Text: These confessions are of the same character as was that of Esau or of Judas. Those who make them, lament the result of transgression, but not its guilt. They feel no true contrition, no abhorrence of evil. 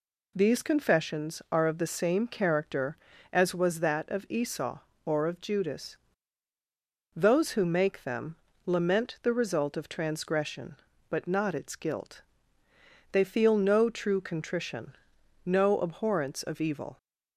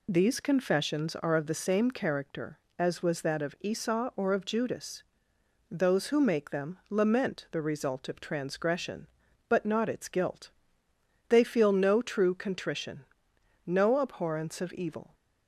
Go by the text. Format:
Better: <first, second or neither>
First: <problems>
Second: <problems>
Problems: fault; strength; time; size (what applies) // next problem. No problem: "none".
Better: neither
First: none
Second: none